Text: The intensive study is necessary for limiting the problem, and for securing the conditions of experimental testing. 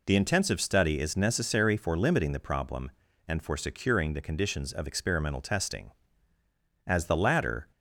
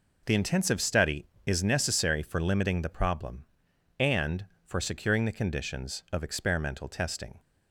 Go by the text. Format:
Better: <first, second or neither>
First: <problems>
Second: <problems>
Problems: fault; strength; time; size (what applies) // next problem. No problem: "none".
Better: second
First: goes on to say "As the latter"; noticeable; from 6.8 s on; 0.82 s long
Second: none